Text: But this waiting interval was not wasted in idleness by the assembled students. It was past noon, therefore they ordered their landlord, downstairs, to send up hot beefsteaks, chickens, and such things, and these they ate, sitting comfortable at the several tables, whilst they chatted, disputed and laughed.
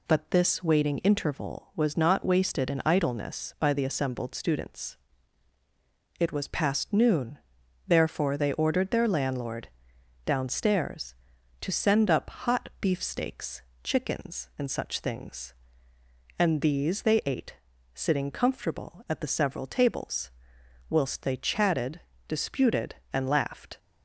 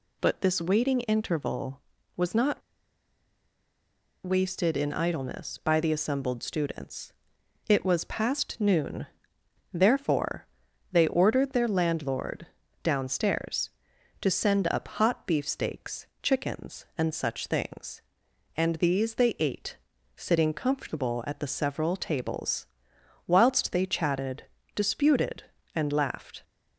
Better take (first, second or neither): first